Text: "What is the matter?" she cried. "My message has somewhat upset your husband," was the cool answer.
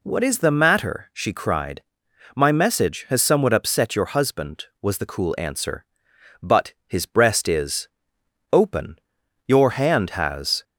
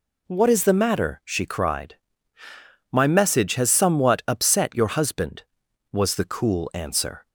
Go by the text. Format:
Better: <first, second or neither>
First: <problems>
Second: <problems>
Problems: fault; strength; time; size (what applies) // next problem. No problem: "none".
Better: second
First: goes on to say "But his breast is open Your hand has"; strong; from 6.4 s on; 4.2 s long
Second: none